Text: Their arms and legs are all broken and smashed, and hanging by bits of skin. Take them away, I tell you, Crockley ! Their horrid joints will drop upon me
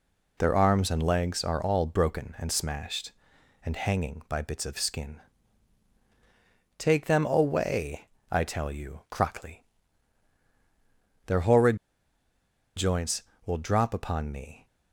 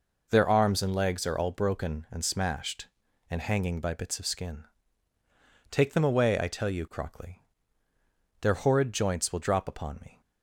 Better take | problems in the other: second | pauses between "horrid" and "joints"; at 11.7 s; 0.99 s long

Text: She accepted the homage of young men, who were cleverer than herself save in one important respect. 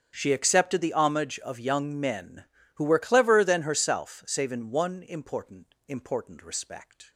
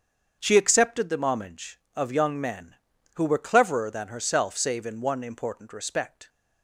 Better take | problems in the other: second | starts louder than the rest; strong; until 1.1 s; 7.5 dB; strong in the second // says "important" twice; at 5.8 s

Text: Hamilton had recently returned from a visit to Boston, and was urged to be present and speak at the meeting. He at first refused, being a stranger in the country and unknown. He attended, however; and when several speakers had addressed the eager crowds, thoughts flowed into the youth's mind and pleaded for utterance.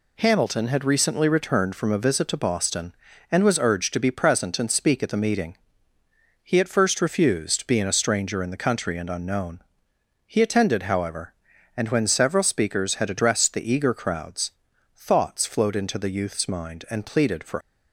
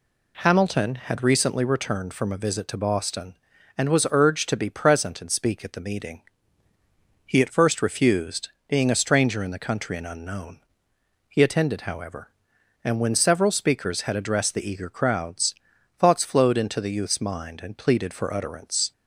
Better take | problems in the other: second | stops before "utterance"; at 17.6 s

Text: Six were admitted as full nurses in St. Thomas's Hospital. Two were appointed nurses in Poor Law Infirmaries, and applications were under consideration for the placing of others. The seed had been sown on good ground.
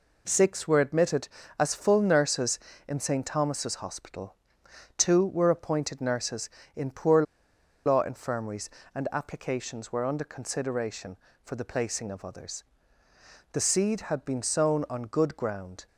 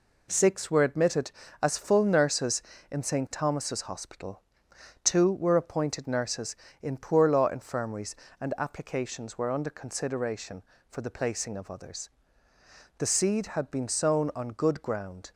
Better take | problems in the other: second | pauses between "Poor" and "Law"; noticeable; at 7.2 s; 0.63 s long

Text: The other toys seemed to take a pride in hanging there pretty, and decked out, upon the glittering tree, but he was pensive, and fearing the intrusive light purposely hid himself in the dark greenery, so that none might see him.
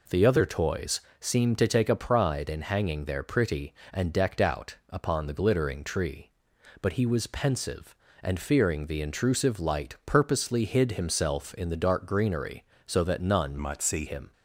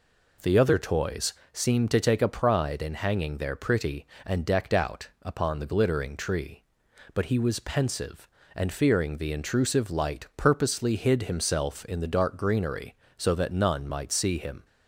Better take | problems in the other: second | pauses between "toys" and "seemed"; slight; at 1.0 s; 0.18 s long; slight in the second // changes voice from "might" to "see"; from 13.5 to 14.0 s; 0.5 s long

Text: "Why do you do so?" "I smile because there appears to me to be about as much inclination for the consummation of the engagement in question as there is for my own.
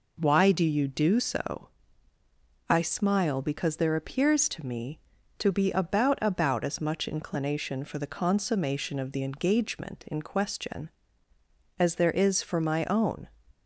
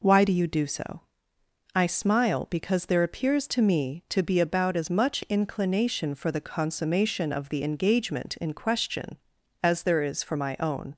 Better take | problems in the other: second | says "about" twice; at 6.2 s

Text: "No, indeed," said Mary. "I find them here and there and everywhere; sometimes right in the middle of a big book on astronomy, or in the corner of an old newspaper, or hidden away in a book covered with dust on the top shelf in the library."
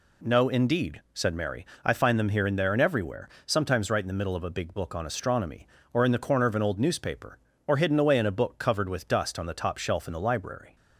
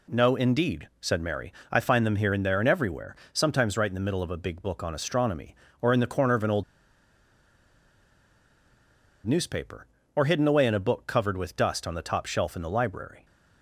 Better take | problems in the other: first | pauses between "old" and "newspaper"; strong; at 6.6 s; 2.6 s long

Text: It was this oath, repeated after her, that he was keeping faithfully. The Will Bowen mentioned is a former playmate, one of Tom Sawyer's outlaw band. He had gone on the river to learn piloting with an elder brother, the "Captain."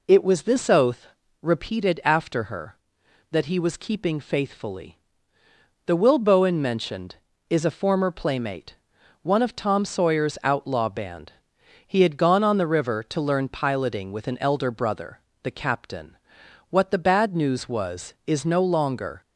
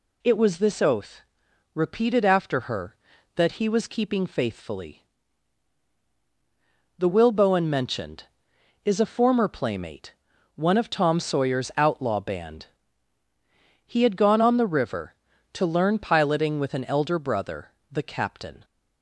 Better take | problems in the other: second | goes on to say "What the bad news was is no longer"; strong; from 16.6 s on; 2.5 s long

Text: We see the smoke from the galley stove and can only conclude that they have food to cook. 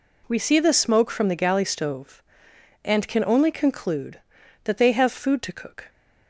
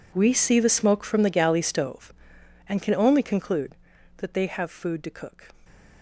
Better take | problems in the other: first | gets quieter; strong; throughout; 19 dB

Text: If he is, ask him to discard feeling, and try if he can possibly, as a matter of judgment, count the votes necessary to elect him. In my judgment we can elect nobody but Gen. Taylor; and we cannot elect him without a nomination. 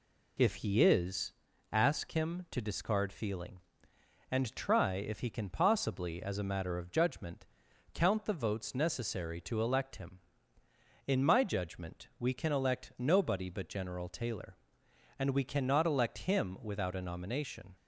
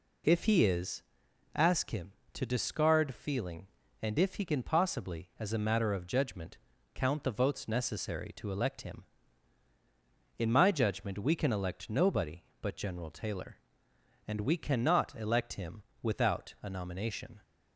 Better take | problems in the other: first | skips "try"; at 4.1 s // pauses between "him" and "without"; slight; at 15.8 s; 0.18 s long

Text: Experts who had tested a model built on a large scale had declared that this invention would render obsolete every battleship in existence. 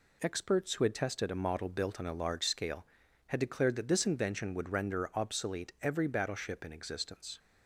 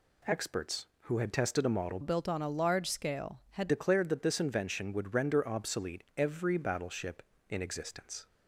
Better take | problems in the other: first | changes voice from "built" to "had"; from 2.0 to 3.6 s; 1.6 s long

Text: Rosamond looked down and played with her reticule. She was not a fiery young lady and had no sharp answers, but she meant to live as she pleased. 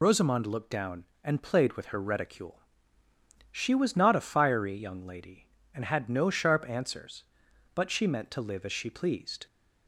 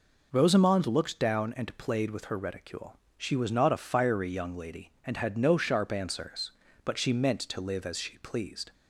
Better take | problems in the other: second | loses the start of "Rosamond"; at 0.0 s; 30 ms

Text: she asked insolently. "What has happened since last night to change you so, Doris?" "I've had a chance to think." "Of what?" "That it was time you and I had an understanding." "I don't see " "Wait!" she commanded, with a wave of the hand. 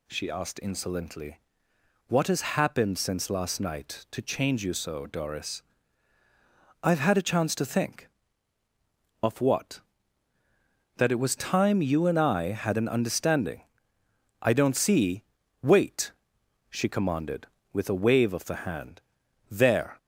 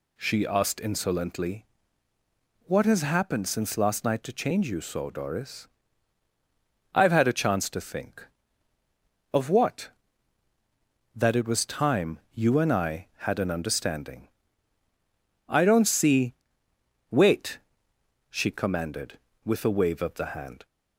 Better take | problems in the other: second | goes on to say "There"; slight; from 19.4 s on; 0.48 s long

